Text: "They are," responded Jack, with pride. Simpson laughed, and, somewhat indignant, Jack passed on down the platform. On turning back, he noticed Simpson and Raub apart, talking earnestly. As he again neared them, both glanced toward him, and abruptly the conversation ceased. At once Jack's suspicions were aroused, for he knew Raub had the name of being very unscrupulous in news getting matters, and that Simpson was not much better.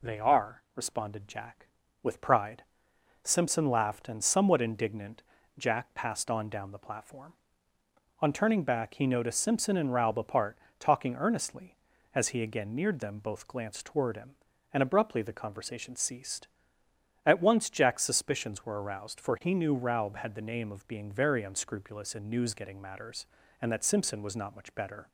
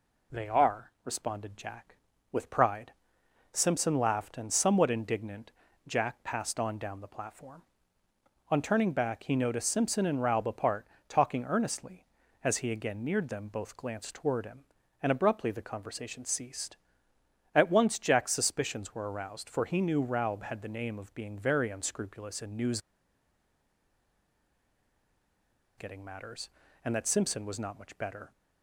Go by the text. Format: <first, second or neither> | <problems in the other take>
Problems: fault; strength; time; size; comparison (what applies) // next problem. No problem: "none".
first | pauses between "news" and "getting"; strong; at 22.7 s; 2.9 s long